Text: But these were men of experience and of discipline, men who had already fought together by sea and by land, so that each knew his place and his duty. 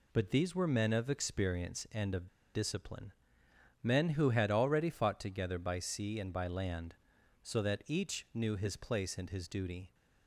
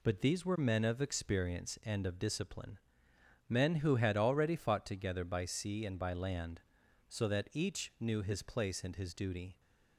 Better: second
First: pauses between "of" and "discipline"; slight; at 2.2 s; 0.26 s long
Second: none

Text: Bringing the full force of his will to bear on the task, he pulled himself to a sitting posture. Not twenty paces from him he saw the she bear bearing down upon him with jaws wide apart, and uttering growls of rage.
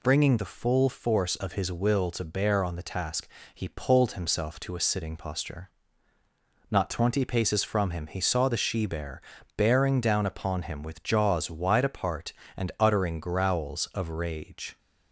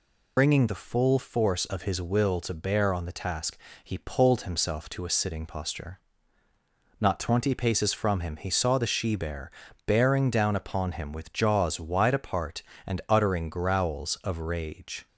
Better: first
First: pauses between "bear" and "bearing"; slight; at 9.2 s; 0.34 s long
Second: loses the start of "Bringing"; at 0.3 s; 40 ms // pauses between "bear" and "bearing"; slight; at 9.5 s; 0.34 s long

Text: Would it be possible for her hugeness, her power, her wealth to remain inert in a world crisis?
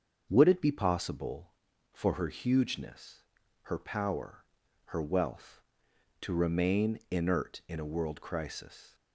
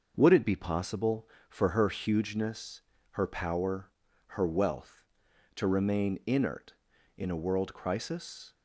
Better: neither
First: starts louder than the rest; until 1.3 s; 7 dB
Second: starts louder than the rest; noticeable; until 1.1 s; 6 dB

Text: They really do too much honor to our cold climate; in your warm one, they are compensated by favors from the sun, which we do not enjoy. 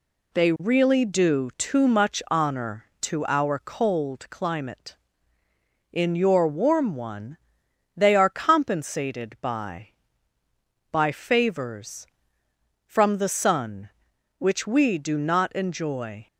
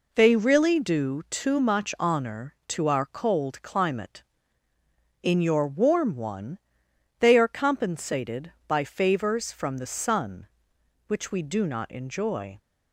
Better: second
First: says "by" twice; at 10.9 s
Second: none

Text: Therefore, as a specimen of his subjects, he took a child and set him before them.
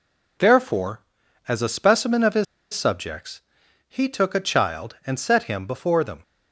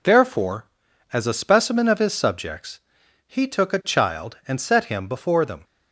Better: second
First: pauses between "his" and "subjects"; slight; at 2.4 s; 0.29 s long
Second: none

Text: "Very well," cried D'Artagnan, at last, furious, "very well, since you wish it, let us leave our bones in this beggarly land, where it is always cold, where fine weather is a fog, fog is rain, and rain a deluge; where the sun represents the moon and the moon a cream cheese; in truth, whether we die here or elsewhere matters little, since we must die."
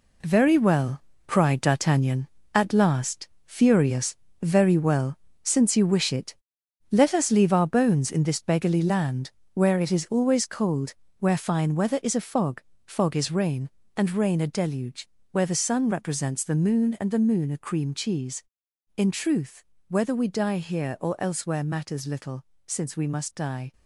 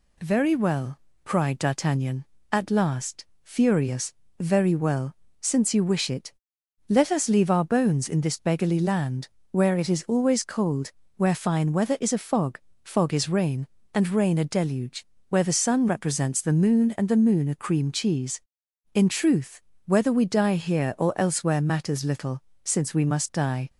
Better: second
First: gets quieter; strong; throughout; 7.5 dB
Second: none

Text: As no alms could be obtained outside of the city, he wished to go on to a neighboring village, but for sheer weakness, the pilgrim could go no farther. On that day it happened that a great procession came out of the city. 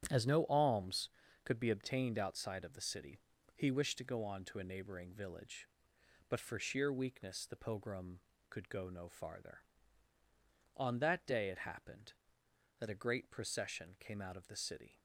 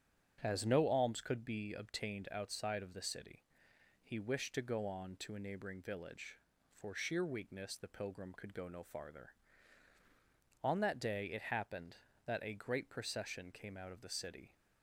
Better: first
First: starts louder than the rest; strong; until 1.5 s; 9 dB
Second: starts louder than the rest; strong; until 1.4 s; 8.5 dB // skips "but"; at 6.5 s

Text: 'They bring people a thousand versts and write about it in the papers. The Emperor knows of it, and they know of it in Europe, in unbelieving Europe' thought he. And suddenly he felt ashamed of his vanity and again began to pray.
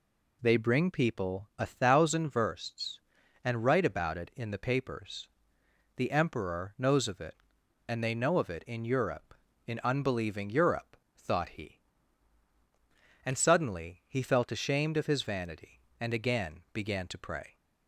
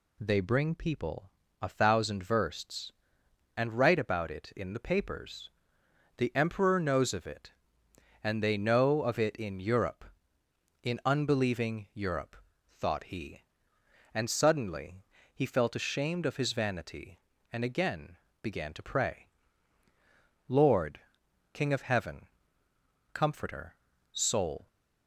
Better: first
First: pauses between "Europe" and "thought"; slight; at 10.9 s; 0.20 s long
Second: pauses between "people" and "a"; slight; at 1.2 s; 0.32 s long // pauses between "Europe" and "thought"; slight; at 12.3 s; 0.36 s long // pauses between "suddenly" and "he"; slight; at 15.0 s; 0.28 s long // pauses between "again" and "began"; slight; at 18.1 s; 0.26 s long // goes on to say "Lord King of Heaven Comforter Soul"; strong; from 20.4 s on; 4.2 s long

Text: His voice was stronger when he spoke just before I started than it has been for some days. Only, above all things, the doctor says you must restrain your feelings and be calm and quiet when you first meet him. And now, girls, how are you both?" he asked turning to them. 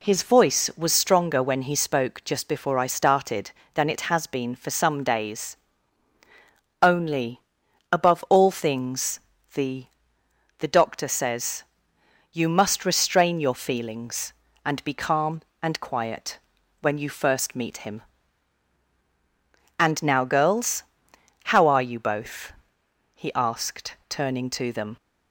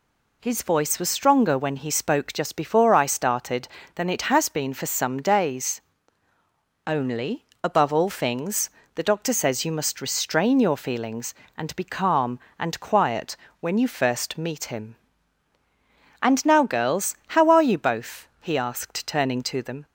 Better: second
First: says "the" twice; at 10.5 s // pauses between "says" and "you"; noticeable; at 11.6 s; 0.70 s long // pauses between "quiet" and "when"; at 16.3 s; 0.42 s long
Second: pauses between "quiet" and "when"; slight; at 13.3 s; 0.24 s long

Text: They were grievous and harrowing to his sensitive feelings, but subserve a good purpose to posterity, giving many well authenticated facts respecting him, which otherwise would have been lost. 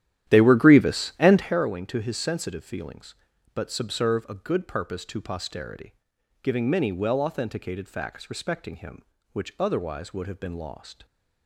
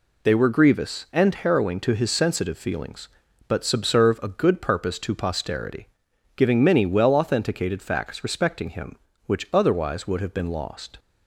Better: second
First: starts louder than the rest; strong; until 1.7 s; 12 dB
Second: none

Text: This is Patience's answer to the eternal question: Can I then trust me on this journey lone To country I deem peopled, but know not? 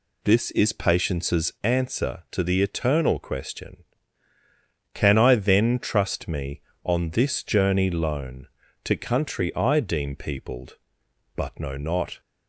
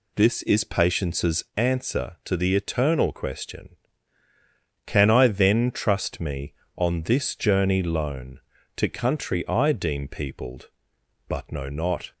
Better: neither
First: none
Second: none

